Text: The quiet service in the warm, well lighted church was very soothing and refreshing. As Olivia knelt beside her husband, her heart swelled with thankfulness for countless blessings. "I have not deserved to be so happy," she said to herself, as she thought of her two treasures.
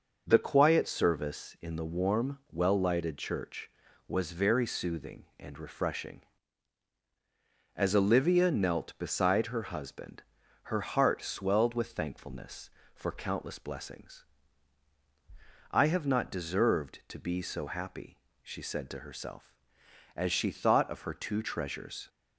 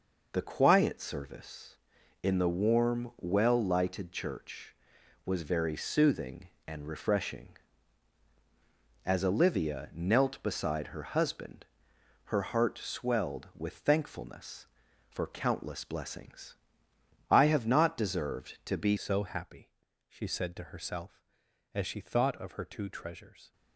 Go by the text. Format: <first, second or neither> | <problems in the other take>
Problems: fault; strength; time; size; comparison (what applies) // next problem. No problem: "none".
first | changes voice at "so"; from 18.9 s on; 4.6 s long